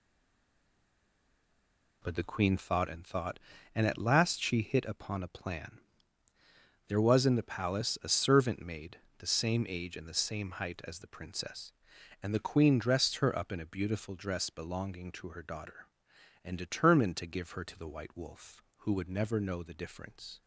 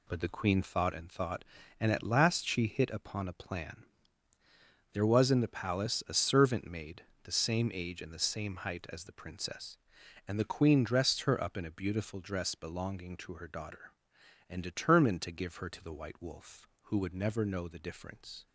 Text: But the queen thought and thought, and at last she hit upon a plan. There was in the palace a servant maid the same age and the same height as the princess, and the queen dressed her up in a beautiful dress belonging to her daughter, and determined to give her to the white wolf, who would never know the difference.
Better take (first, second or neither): second